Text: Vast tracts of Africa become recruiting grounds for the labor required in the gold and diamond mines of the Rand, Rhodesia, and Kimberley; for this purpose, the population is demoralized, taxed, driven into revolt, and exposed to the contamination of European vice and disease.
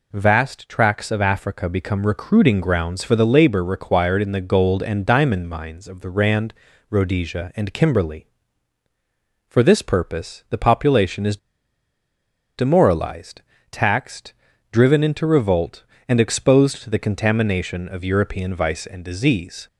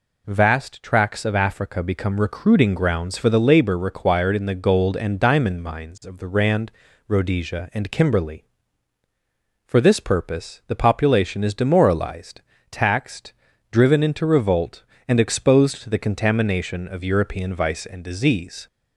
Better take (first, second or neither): second